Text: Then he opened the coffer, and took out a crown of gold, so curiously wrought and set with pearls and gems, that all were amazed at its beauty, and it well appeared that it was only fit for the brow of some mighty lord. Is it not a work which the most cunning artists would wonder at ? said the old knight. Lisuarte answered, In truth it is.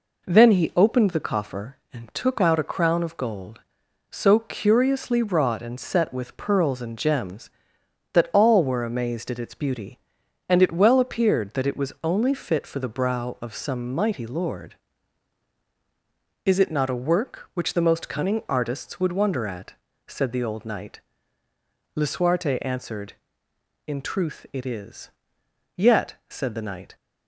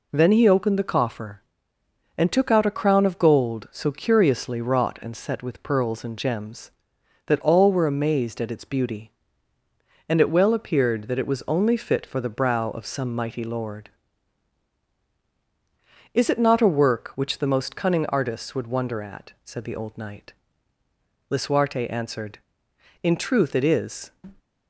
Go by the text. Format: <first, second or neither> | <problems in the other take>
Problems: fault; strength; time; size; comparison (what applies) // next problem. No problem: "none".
second | goes on to say "Yet said the knight"; noticeable; from 25.7 s on; 1.2 s long